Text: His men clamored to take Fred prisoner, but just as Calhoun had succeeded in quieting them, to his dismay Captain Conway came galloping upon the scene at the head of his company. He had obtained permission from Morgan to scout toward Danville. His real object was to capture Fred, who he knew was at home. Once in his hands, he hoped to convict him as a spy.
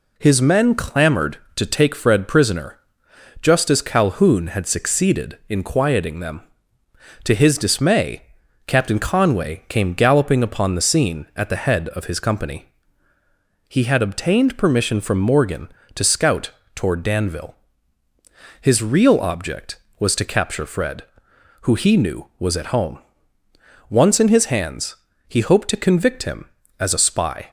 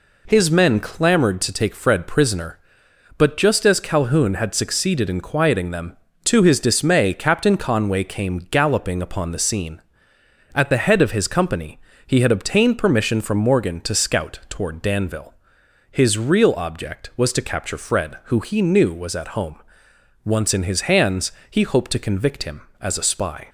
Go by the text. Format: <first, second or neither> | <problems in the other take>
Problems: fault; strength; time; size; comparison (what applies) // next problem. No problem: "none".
second | skips "but"; at 3.0 s // pauses between "dismay" and "Captain"; at 8.2 s; 0.44 s long // pauses between "scout" and "toward"; slight; at 16.4 s; 0.24 s long